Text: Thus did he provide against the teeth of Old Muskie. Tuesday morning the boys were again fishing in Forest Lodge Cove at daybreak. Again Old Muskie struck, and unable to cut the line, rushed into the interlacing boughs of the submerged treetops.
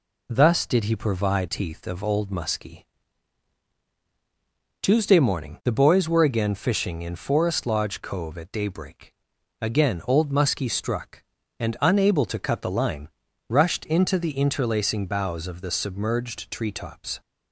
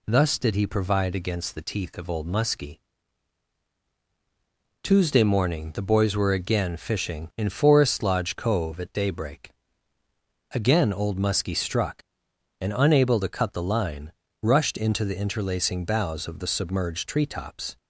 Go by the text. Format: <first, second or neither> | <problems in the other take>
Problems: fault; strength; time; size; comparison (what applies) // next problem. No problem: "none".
second | skips "against the"; at 1.4 s